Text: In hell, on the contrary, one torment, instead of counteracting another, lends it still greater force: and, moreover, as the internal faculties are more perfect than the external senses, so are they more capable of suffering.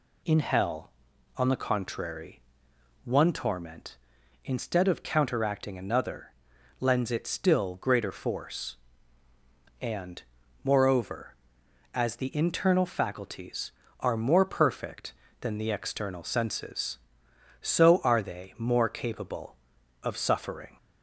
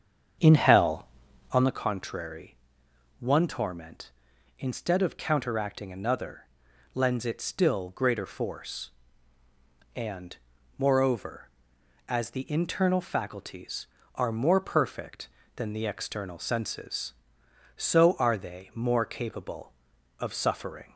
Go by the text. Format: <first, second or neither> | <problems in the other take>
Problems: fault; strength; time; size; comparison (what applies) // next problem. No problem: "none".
first | starts louder than the rest; strong; until 1.7 s; 7.5 dB